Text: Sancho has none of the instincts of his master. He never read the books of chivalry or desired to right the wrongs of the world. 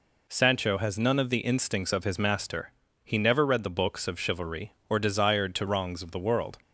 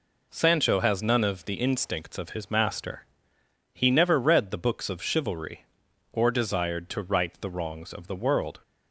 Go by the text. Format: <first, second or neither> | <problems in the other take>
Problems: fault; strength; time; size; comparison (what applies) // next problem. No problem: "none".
second | skips "right the"; at 5.6 s